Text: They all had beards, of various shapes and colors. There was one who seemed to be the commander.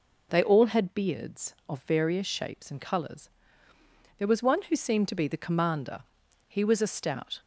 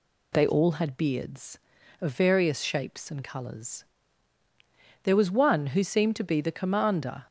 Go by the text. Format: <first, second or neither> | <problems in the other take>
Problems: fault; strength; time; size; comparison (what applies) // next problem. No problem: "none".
second | goes on to say "He was a stout"; noticeable; from 6.4 s on; 0.92 s long